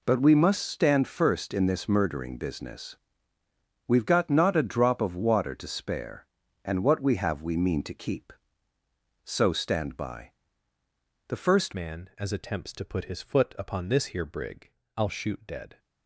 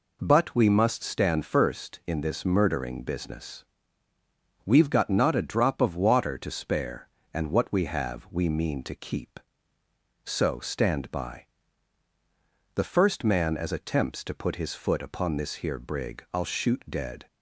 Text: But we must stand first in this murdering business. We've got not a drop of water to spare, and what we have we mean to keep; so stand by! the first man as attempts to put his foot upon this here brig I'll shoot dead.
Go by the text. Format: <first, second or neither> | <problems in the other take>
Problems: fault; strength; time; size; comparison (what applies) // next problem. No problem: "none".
second | changes voice at "man"; from 11.7 s on; 4.0 s long // pauses between "brig" and "I'll"; slight; at 14.7 s; 0.26 s long